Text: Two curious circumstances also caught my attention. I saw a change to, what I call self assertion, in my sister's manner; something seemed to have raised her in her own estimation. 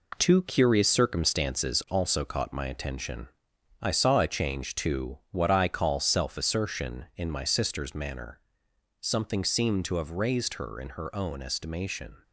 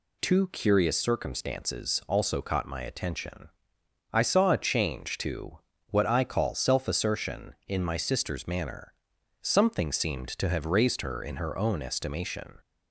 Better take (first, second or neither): second